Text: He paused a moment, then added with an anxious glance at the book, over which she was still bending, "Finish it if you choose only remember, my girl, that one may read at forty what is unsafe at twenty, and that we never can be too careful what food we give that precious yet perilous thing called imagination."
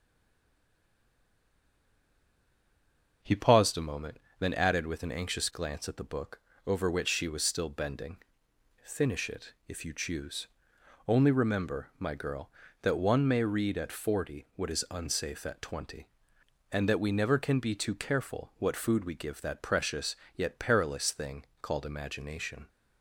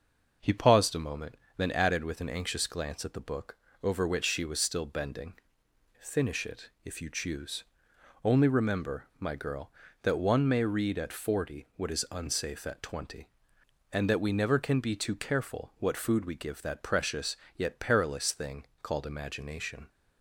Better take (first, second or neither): second